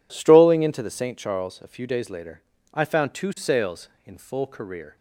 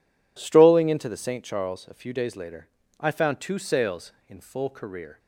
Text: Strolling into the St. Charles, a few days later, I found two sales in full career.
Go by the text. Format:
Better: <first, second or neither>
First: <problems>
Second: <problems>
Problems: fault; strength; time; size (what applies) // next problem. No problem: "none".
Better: neither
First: none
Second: none